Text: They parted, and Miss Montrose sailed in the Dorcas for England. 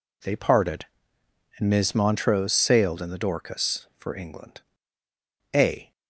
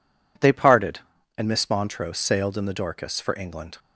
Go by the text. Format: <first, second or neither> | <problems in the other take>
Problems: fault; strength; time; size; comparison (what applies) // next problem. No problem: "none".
second | goes on to say "A"; slight; from 5.5 s on; 0.36 s long